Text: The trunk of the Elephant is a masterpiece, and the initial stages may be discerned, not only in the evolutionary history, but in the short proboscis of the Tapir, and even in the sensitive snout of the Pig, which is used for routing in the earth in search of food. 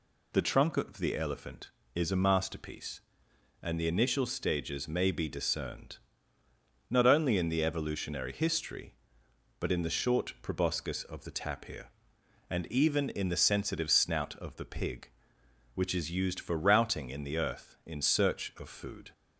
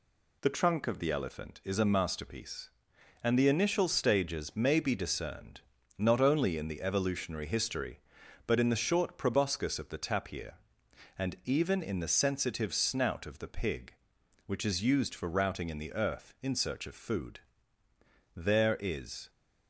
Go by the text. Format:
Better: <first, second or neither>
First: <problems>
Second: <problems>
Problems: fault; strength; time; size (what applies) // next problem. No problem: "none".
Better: first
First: none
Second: goes on to say "There is"; noticeable; from 18.3 s on; 0.94 s long